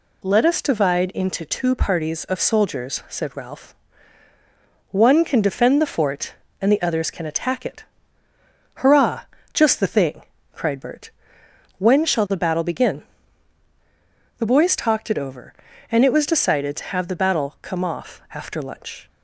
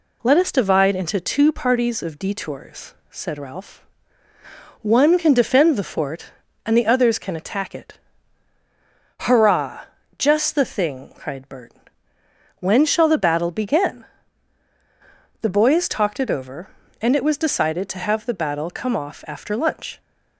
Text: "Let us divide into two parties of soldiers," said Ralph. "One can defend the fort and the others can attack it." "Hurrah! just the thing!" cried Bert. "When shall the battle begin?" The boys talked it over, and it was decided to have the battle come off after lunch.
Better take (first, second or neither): first